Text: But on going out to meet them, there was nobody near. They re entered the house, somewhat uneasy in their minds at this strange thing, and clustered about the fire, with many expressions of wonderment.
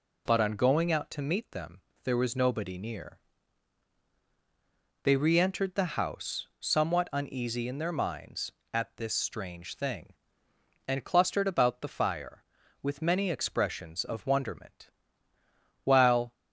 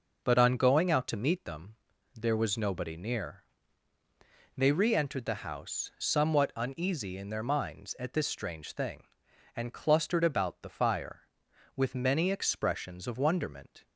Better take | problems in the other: second | goes on to say "While"; slight; from 15.8 s on; 0.48 s long

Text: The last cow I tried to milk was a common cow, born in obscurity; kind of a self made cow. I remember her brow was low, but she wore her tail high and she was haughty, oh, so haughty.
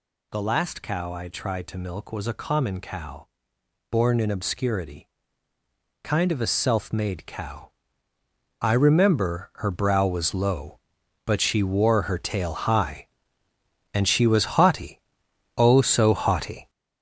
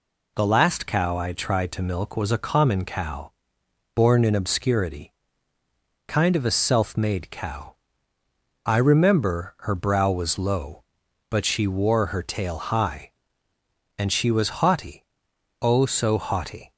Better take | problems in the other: second | gets louder; throughout; 7 dB

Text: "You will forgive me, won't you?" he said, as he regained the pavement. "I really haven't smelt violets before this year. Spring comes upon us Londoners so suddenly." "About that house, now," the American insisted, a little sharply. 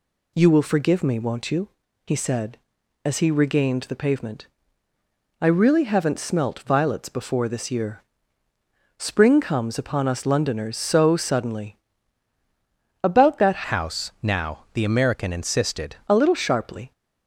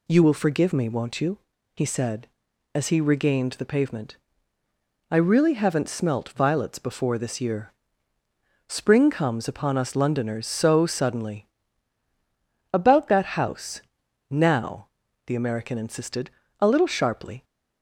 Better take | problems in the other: second | changes voice from "house" to "insisted"; from 13.6 to 15.9 s; 2.3 s long

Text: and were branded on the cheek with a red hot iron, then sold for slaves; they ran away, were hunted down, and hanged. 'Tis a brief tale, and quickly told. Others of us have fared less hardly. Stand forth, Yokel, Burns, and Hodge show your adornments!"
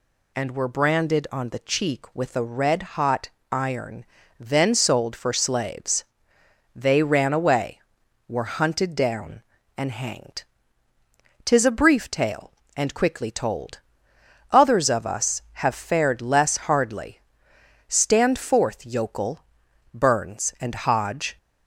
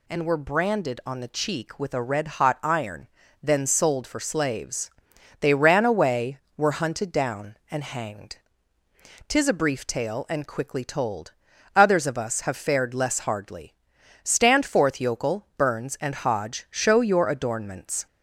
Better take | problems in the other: second | pauses between "hot" and "iron"; slight; at 3.2 s; 0.22 s long // stops before "show your adornments"; at 21.3 s

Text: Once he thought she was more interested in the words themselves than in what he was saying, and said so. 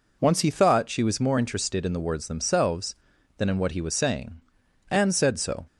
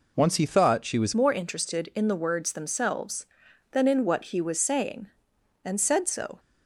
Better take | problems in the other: first | changes voice at "more"; from 1.1 s on; 5.2 s long

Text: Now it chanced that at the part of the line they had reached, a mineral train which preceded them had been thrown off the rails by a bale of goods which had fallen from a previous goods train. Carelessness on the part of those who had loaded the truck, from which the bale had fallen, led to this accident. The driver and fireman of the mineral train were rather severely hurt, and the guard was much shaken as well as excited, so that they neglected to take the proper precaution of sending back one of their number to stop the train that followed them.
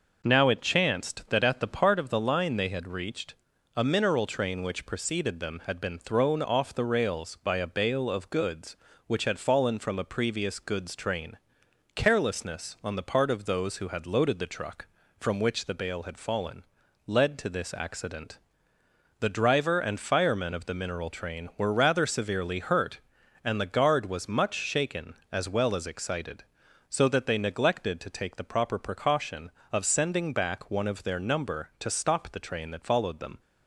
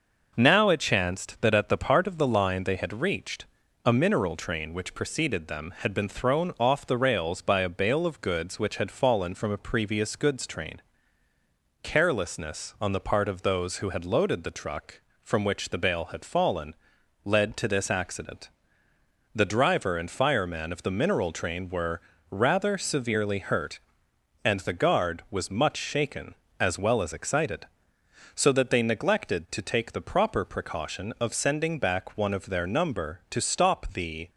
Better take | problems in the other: first | pauses between "were" and "rather"; slight; at 22.0 s; 0.30 s long // stops before "train that followed them"; at 34.2 s

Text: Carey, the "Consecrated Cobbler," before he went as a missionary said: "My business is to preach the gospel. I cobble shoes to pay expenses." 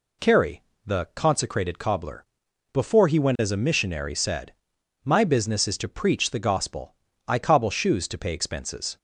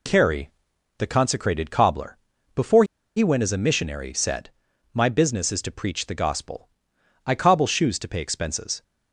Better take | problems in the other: first | pauses between "before" and "he"; slight; at 2.8 s; 0.31 s long

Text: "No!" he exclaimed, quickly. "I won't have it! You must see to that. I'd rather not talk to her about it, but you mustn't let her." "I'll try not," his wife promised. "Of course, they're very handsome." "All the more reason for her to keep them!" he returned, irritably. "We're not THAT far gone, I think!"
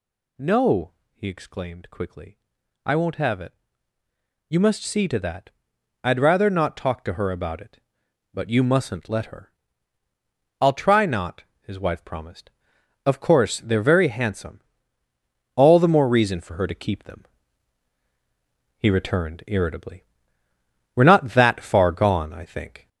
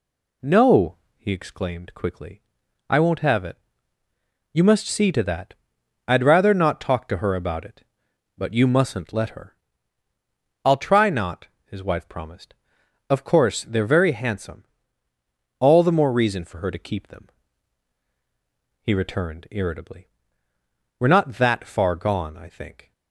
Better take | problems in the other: second | gets louder; noticeable; throughout; 4 dB

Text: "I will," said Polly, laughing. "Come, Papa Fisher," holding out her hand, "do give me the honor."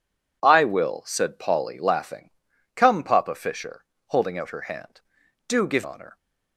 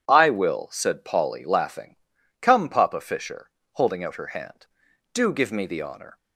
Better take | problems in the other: second | skips "me the"; at 5.8 s

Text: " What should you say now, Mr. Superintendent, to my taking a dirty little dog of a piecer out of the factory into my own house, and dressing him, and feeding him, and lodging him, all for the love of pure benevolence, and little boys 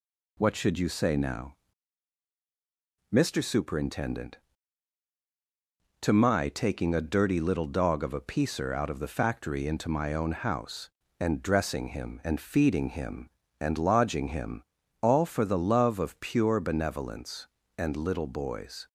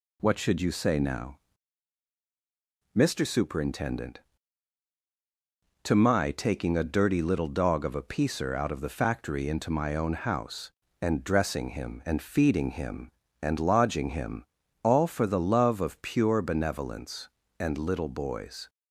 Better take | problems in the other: neither | none

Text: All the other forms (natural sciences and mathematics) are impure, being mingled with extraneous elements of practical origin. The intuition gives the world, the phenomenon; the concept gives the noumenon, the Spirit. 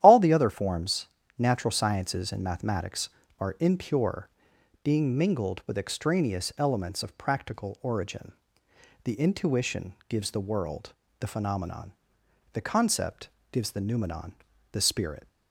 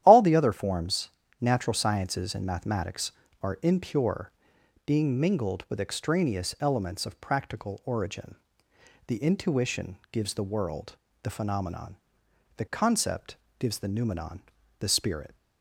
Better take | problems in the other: neither | starts louder than the rest; strong; the same in both // pauses between "concept" and "gives"; slight; the same in both

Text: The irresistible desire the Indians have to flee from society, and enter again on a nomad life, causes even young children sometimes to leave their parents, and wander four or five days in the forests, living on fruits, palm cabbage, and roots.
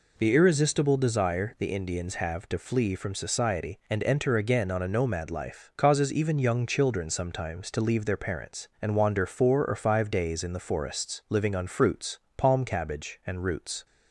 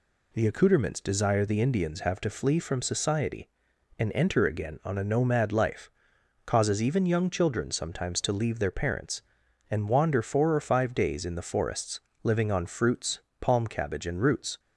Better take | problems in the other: first | says "accouterments" for "irresistible"; at 0.4 s

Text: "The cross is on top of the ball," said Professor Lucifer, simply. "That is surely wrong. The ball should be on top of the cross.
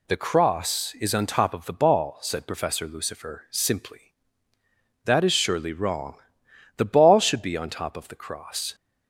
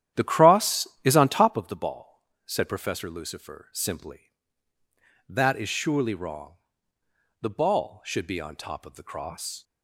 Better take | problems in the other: first | starts louder than the rest; strong; until 1.6 s; 11 dB

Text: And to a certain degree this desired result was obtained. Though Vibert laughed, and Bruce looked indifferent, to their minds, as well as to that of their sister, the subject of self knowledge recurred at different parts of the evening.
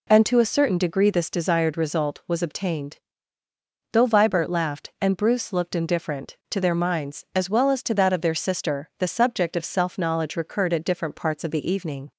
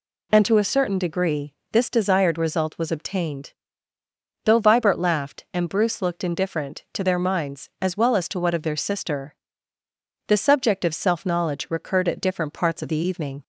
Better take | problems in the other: first | pauses between "degree" and "this"; slight; at 1.5 s; 0.18 s long // says "what" for "that"; at 8.3 s

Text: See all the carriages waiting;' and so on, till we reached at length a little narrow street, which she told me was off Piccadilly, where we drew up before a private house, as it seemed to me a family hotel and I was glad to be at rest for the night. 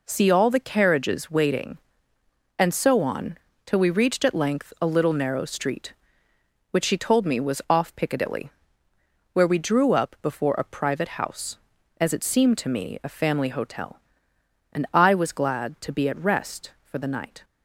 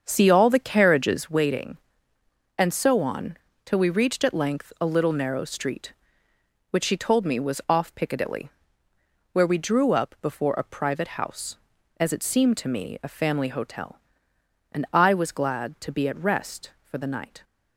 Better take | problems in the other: first | starts louder than the rest; until 1.4 s; 7 dB

